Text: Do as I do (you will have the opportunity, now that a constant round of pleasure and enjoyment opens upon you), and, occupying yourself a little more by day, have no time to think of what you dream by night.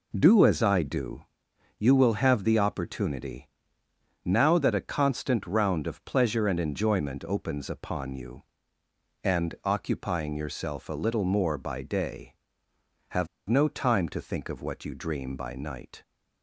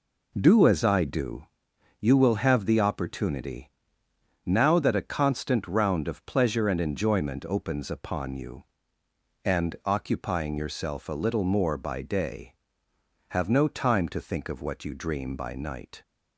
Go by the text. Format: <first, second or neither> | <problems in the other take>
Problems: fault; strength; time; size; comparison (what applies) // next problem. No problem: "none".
second | pauses between "have" and "no"; slight; at 13.2 s; 0.22 s long